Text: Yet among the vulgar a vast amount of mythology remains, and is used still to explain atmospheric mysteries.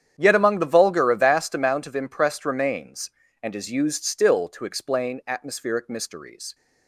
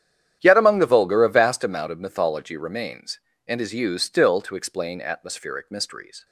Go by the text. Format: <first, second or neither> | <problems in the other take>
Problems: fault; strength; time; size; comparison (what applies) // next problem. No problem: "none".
second | starts louder than the rest; strong; until 1.1 s; 9 dB; strong in the second // says "impressed" for "mythology"; at 1.9 s